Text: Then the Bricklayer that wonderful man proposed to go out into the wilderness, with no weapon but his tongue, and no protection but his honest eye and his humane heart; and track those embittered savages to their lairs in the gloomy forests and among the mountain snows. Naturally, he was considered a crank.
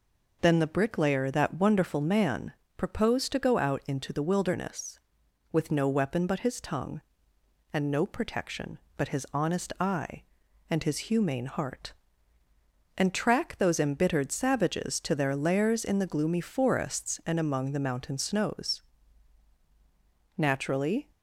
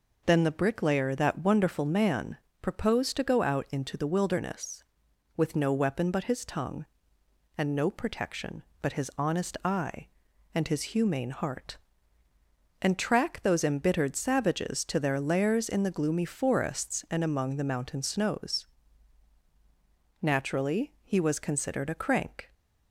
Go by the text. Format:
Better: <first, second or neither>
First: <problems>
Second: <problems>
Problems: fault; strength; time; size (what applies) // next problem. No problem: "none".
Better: second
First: pauses between "man" and "proposed"; slight; at 2.5 s; 0.24 s long // stops before "he was considered a crank"; at 21.1 s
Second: pauses between "man" and "proposed"; slight; at 2.3 s; 0.24 s long